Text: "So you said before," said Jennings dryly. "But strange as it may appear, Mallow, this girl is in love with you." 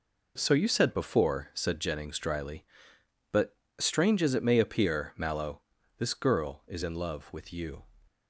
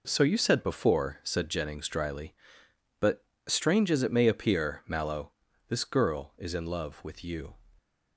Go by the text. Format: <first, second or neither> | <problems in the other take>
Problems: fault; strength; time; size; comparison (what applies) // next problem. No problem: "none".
neither | pauses between "But" and "strange"; slight; the same in both